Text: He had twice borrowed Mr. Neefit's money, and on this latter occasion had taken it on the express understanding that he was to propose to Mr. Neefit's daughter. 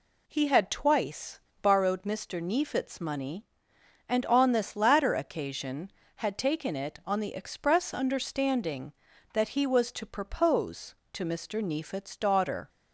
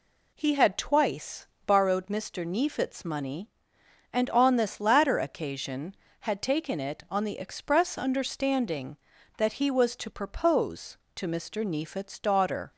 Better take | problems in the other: neither | pauses between "twice" and "borrowed"; slight; the same in both

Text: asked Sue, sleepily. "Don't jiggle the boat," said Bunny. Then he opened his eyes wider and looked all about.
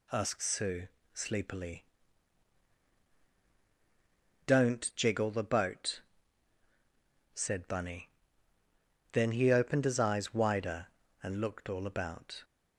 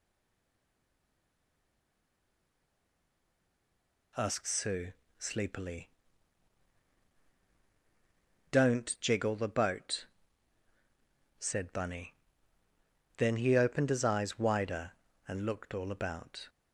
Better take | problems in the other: first | stays silent before the first word; strong; until 4.1 s; 4.1 s long

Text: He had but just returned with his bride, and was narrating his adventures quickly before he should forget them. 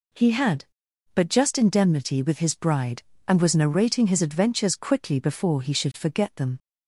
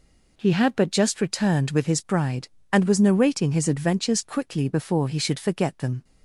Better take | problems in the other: second | says "indemnity" for "returned"; at 1.5 s

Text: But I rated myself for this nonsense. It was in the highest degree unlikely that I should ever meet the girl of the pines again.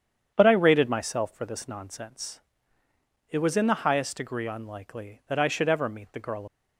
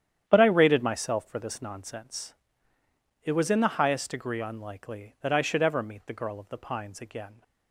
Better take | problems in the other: second | starts louder than the rest; strong; until 1.3 s; 8.5 dB; strong in the second // stops before "of the pines again"; at 6.4 s

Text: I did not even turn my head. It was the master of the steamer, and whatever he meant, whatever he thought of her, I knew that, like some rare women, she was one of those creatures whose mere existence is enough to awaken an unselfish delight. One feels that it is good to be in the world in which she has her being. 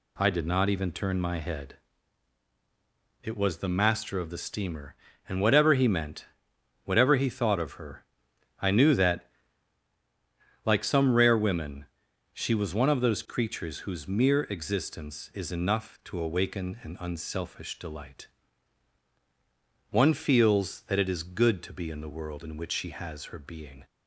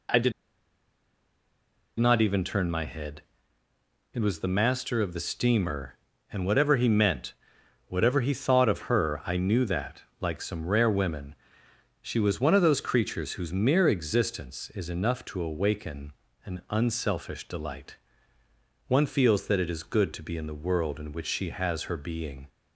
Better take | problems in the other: first | pauses between "did" and "not"; strong; at 0.3 s; 1.6 s long // pauses between "awaken" and "an"; slight; at 16.1 s; 0.32 s long

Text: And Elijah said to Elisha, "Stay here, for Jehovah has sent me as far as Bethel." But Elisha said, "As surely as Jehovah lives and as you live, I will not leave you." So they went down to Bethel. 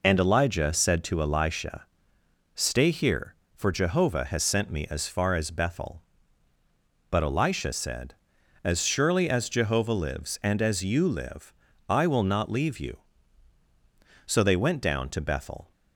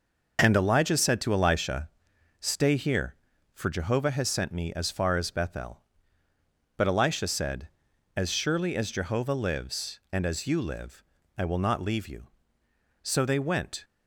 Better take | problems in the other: first | stops before "down to Bethel"; at 13.8 s

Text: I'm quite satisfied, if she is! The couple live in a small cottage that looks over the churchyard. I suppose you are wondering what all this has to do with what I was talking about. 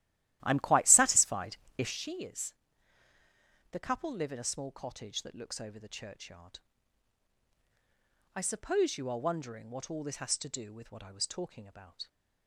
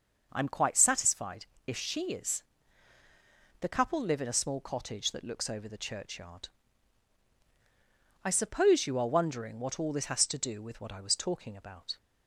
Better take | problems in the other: second | starts louder than the rest; strong; until 2.0 s; 13.5 dB

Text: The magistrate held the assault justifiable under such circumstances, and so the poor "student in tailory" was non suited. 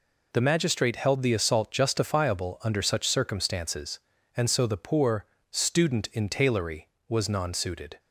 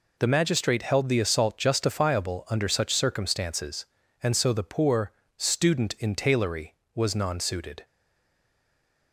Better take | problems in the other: first | pauses between "poor" and "student"; slight; at 5.1 s; 0.26 s long; slight in the first // stays silent after the last word; noticeable; from 7.8 s on; 1.3 s long

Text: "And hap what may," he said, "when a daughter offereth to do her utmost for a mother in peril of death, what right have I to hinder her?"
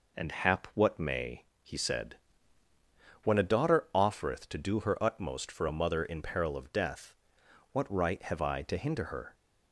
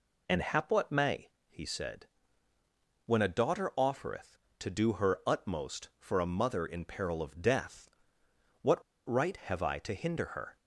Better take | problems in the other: first | pauses between "what" and "right"; slight; at 8.8 s; 0.24 s long

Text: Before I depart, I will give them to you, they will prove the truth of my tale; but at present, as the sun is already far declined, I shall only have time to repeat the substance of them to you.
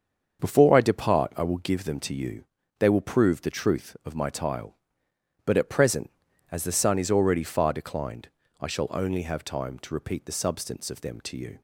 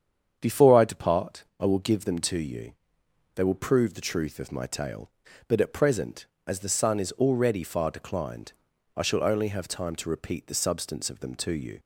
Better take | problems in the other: second | starts louder than the rest; until 1.4 s; 7 dB; strong in the second // says "tile" for "tale"; at 4.3 s

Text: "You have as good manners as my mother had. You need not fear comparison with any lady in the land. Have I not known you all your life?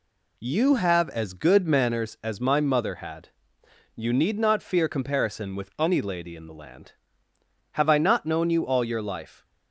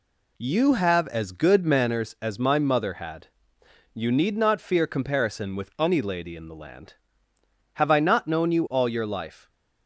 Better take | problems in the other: neither | none

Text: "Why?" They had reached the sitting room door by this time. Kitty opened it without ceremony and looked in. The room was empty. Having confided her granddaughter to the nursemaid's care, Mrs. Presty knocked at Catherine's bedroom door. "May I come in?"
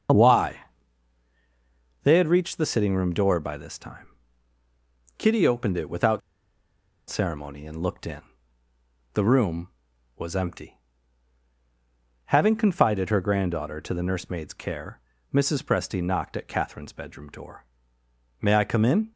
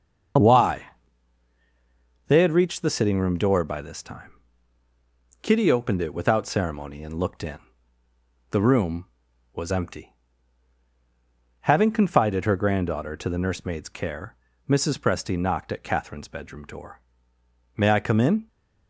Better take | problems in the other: second | starts louder than the rest; until 2.5 s; 6.5 dB; also in the second // pauses between "without" and "ceremony"; noticeable; at 6.2 s; 0.89 s long

